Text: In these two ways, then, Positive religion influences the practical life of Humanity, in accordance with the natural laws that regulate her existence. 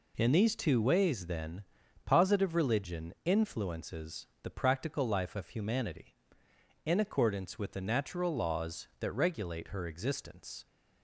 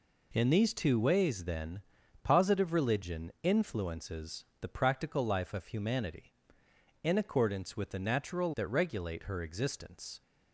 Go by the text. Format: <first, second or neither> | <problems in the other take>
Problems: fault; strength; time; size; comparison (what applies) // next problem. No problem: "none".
first | pauses between "influences" and "the"; slight; at 4.4 s; 0.16 s long; slight in the first // skips "laws"; at 8.5 s